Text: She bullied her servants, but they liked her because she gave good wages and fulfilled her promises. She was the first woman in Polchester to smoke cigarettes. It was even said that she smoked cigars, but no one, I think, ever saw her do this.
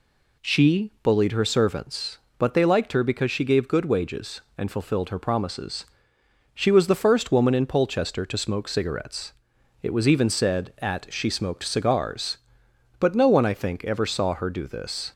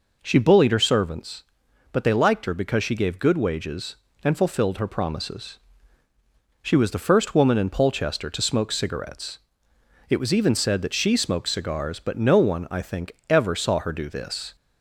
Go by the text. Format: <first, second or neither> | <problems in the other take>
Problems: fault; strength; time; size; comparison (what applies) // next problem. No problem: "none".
second | says "at" for "that"; at 10.7 s